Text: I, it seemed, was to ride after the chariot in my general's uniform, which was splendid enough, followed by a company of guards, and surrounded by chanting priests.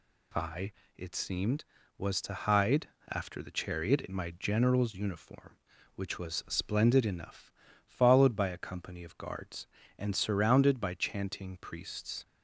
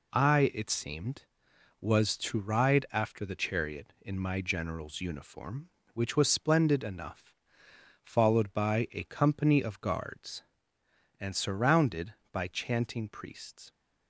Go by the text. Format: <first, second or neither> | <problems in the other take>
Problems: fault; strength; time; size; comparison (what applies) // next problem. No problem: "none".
second | says "hide" for "ride"; at 2.3 s